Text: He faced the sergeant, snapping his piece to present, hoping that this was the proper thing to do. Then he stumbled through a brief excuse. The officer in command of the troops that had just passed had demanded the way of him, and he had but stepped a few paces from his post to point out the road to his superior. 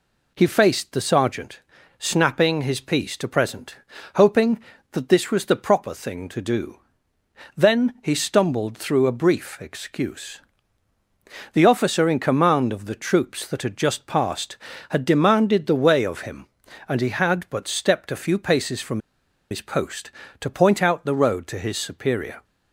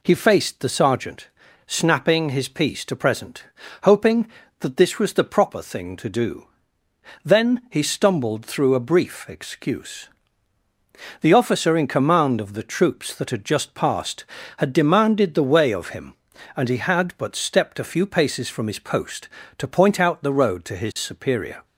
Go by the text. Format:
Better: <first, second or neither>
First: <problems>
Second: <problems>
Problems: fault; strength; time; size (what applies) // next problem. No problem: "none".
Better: second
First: pauses between "from" and "his"; noticeable; at 18.9 s; 0.51 s long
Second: none